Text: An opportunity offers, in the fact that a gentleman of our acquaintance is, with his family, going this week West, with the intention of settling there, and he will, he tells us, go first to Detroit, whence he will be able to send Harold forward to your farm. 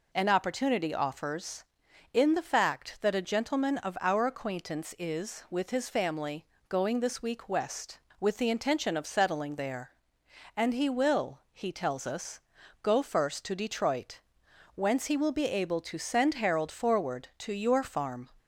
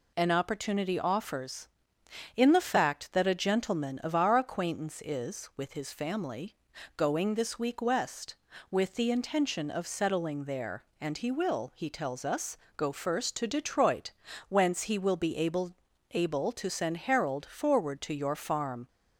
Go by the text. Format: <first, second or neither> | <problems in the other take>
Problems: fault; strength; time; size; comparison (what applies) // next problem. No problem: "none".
first | says "able" twice; at 16.1 s